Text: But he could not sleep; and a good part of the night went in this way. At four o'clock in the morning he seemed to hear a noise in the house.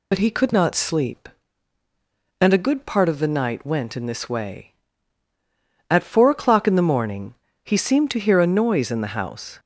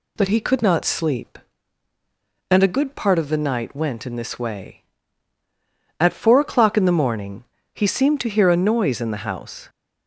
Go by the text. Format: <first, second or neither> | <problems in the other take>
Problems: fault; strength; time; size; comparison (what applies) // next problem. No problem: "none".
second | loses the start of "But"; at 0.1 s; 45 ms // pauses between "morning" and "he"; slight; at 7.3 s; 0.32 s long; slight in the second